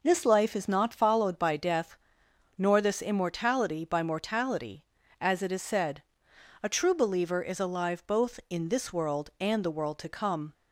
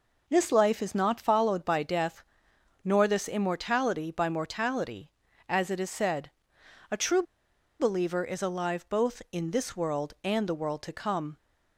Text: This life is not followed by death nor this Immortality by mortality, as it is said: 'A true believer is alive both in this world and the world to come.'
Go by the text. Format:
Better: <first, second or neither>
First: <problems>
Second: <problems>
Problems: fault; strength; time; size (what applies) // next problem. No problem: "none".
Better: first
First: pauses between "death" and "nor"; noticeable; at 1.9 s; 0.60 s long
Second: pauses between "death" and "nor"; noticeable; at 2.2 s; 0.60 s long // pauses between "true" and "believer"; noticeable; at 7.2 s; 0.57 s long